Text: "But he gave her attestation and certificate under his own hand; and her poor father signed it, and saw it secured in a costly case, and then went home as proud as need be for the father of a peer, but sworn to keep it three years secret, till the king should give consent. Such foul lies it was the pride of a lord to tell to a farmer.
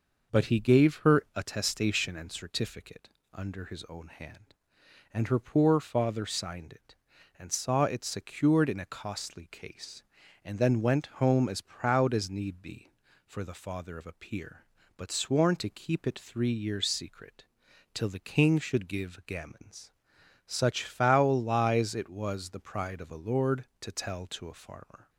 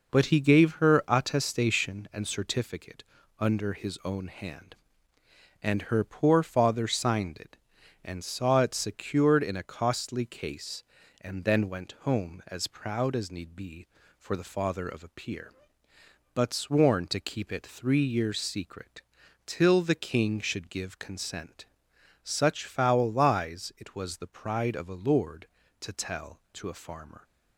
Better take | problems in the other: second | pauses between "certificate" and "under"; slight; at 3.0 s; 0.24 s long; slight in the second // says "gammons" for "consent"; at 19.2 s

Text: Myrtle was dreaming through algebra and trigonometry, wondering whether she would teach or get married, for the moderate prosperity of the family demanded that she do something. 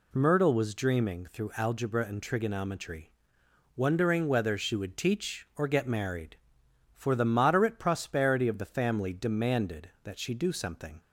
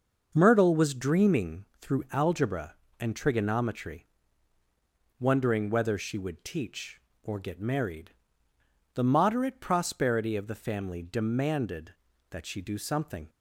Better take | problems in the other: first | starts louder than the rest; until 1.3 s; 6 dB // skips "for"; at 8.5 s

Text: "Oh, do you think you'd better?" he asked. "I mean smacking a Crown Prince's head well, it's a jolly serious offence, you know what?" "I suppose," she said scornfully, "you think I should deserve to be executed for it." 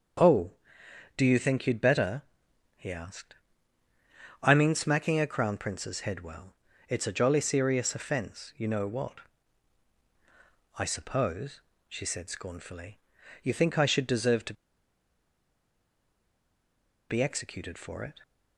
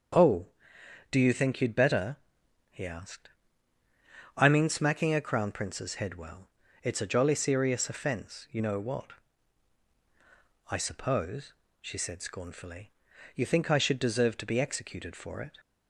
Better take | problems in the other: second | starts louder than the rest; strong; until 1.8 s; 7 dB; strong in the second // pauses between "to" and "be"; strong; at 14.5 s; 2.5 s long

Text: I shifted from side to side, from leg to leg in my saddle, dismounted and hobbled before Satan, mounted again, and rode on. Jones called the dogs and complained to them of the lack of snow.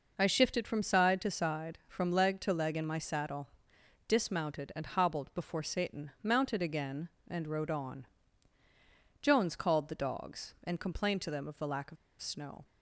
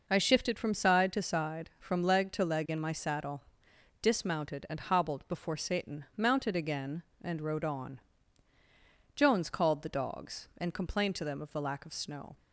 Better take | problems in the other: second | pauses between "of" and "snow"; slight; at 11.9 s; 0.25 s long

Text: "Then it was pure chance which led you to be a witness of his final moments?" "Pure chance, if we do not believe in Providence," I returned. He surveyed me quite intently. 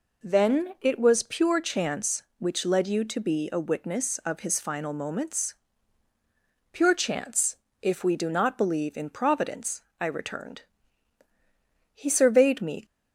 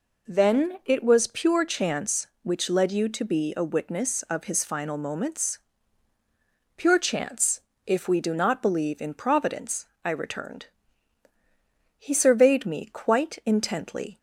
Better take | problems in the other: second | stops before "quite intently"; at 12.8 s

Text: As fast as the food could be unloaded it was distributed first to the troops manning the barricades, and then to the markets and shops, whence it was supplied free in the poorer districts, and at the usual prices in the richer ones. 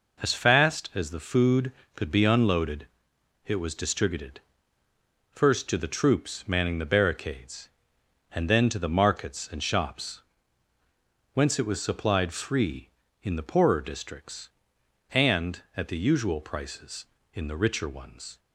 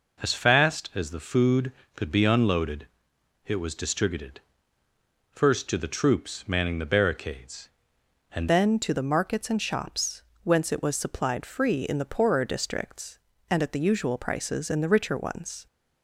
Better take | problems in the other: first | pauses between "unloaded" and "it"; noticeable; at 2.8 s; 0.60 s long; noticeable in the first // pauses between "distributed" and "first"; noticeable; at 4.4 s; 0.90 s long; noticeable in the first // changes voice at "then"; from 8.4 s on; 7.2 s long

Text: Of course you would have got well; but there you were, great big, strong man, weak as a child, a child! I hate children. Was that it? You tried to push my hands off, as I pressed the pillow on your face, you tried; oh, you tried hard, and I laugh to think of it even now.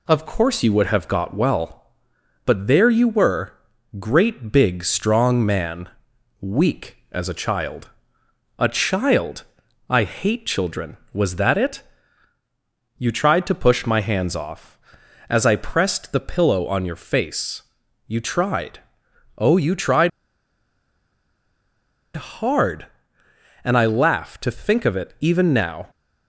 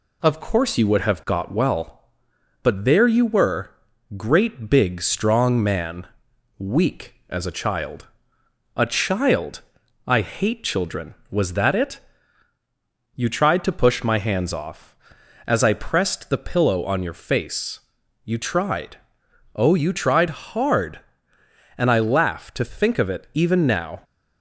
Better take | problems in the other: second | pauses between "tried" and "hard"; strong; at 20.0 s; 2.0 s long

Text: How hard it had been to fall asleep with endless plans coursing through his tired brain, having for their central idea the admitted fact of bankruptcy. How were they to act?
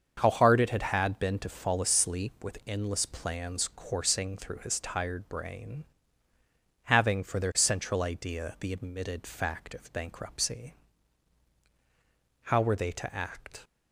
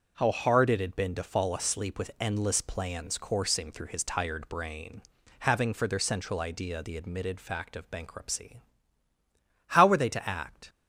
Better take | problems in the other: second | starts louder than the rest; until 1.2 s; 7 dB // says "had" twice; at 0.8 s

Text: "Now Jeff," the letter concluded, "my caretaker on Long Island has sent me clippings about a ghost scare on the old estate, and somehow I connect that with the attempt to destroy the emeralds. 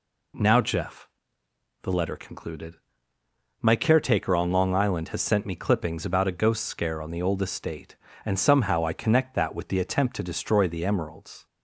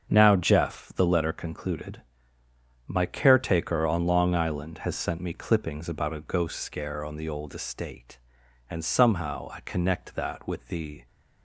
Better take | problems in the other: first | starts louder than the rest; strong; until 1.1 s; 7 dB // stops before "attempt to destroy the emeralds"; at 11.0 s

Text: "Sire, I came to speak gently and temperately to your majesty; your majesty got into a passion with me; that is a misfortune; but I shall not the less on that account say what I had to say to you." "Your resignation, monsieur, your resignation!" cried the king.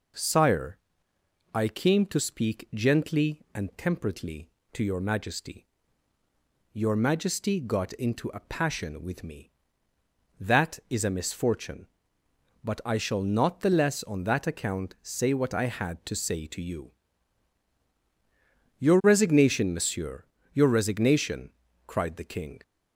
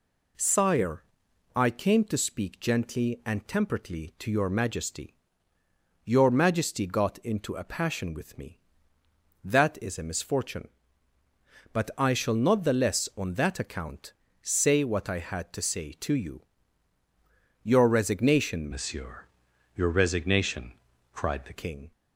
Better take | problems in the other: first | pauses between "account" and "say"; slight; at 14.1 s; 0.30 s long // changes voice from "monsieur" to "the"; from 18.7 to 21.5 s; 2.8 s long

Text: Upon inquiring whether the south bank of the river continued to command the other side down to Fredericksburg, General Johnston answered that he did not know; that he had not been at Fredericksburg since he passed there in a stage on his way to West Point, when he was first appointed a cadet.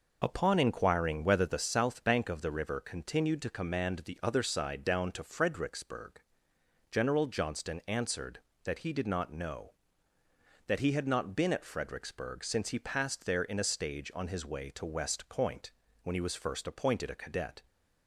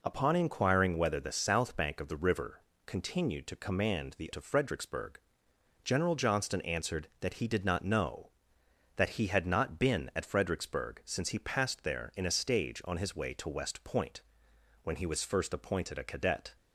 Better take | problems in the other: first | pauses between "river" and "continued"; slight; at 2.6 s; 0.26 s long // skips "other side down"; at 4.3 s

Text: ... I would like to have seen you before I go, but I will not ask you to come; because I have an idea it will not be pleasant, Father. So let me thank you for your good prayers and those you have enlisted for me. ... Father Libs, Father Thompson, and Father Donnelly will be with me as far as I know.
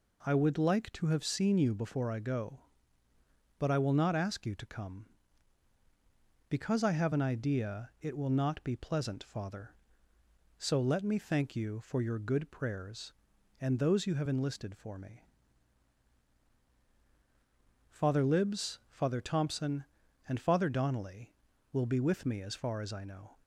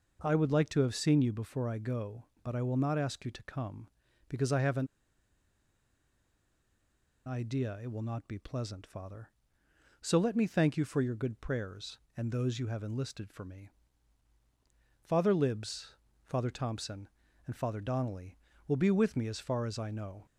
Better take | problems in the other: first | pauses between "an" and "idea"; strong; at 4.8 s; 2.3 s long

